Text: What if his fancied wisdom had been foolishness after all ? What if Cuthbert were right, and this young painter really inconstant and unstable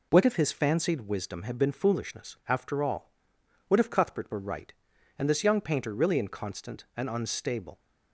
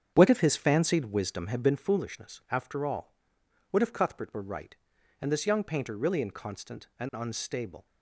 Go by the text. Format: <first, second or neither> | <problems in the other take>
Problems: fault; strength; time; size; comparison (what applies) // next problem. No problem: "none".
first | starts louder than the rest; strong; until 1.8 s; 8 dB